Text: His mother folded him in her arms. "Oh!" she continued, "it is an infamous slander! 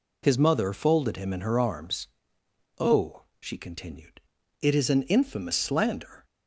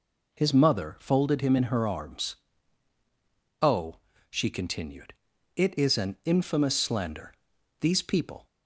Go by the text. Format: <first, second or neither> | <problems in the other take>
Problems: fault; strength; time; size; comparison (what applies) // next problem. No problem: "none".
first | goes on to say "These people"; noticeable; from 7.8 s on; 0.66 s long